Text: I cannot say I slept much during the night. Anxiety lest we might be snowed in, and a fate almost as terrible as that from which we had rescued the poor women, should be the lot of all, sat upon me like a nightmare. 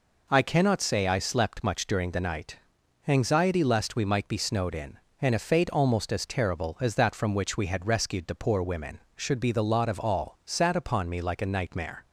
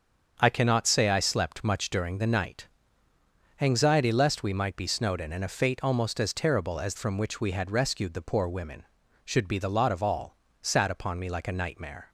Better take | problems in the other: first | starts louder than the rest; strong; until 1.4 s; 7 dB // skips "that"; at 6.9 s

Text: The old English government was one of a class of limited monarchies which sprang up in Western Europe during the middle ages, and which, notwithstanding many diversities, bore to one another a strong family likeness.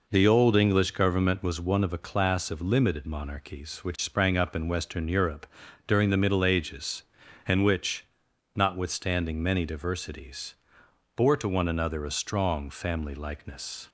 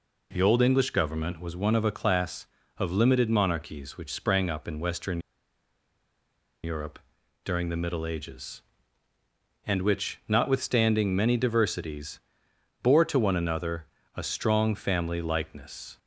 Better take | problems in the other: first | pauses between "Western" and "Europe"; strong; at 5.1 s; 1.4 s long // pauses between "Europe" and "during"; at 6.9 s; 0.44 s long; also in the first // pauses between "another" and "a"; slight; at 13.8 s; 0.28 s long

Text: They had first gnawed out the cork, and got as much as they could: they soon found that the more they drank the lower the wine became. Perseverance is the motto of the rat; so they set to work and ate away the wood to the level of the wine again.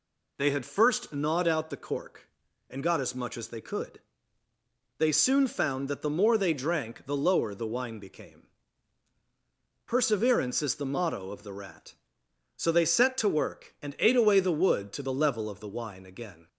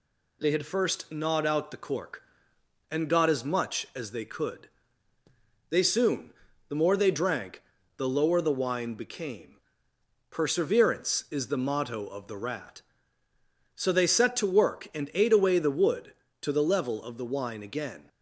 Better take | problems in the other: first | skips "found that"; at 6.5 s // pauses between "drank" and "the"; slight; at 7.6 s; 0.36 s long

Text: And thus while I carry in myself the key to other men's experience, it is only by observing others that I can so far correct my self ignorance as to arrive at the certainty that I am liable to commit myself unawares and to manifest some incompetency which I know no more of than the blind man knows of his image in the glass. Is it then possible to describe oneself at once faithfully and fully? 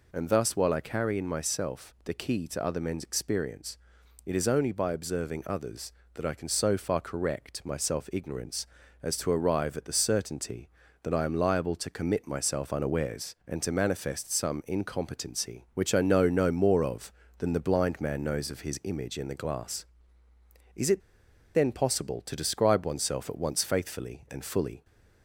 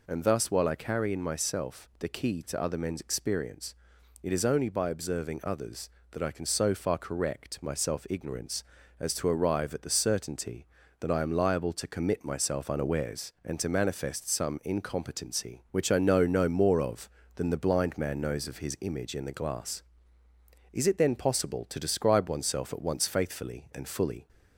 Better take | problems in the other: second | pauses between "it" and "then"; noticeable; at 21.0 s; 0.53 s long

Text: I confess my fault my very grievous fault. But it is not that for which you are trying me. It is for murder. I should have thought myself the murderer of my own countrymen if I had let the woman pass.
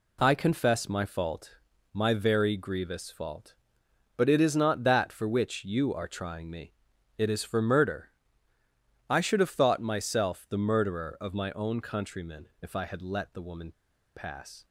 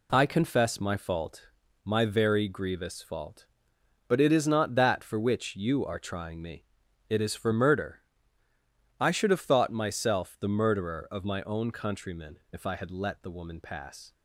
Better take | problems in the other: second | pauses between "fault" and "my"; at 1.5 s; 0.38 s long; also in the second // pauses between "countrymen" and "if"; slight; at 12.4 s; 0.16 s long; slight in the second // pauses between "woman" and "pass"; at 13.7 s; 0.43 s long

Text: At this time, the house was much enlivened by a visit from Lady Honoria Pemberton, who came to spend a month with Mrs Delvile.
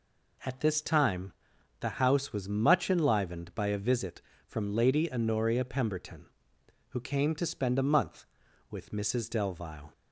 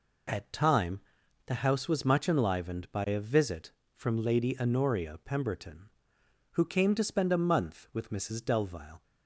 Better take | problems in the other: first | skips "this"; at 0.5 s

